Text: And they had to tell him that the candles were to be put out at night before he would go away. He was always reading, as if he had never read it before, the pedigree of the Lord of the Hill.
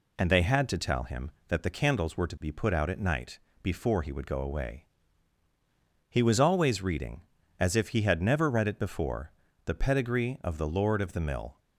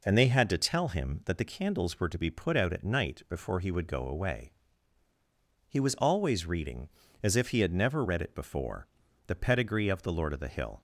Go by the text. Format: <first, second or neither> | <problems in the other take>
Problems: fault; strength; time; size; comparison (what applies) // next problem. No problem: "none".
second | pauses between "night" and "before"; slight; at 3.3 s; 0.24 s long // says "Mill" for "Hill"; at 11.2 s